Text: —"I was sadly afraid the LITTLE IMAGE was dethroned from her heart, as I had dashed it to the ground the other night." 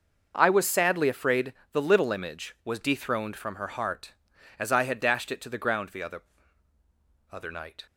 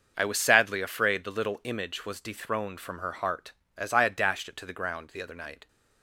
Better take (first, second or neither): second